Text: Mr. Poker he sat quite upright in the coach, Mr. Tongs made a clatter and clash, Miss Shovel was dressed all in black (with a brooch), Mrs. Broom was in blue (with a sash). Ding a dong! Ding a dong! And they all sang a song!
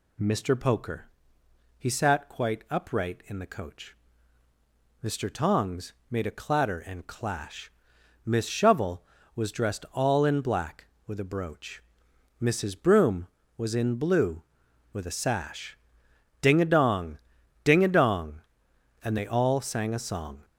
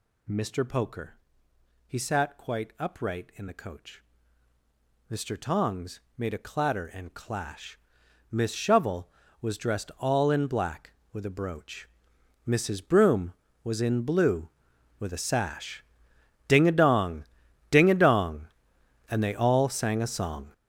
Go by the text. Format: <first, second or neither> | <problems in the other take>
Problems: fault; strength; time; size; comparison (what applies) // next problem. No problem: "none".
first | gets louder; strong; throughout; 12 dB // pauses between "Poker" and "he"; noticeable; at 1.1 s; 0.72 s long; noticeable in the first // pauses between "Tongs" and "made"; slight; at 5.9 s; 0.18 s long; slight in the first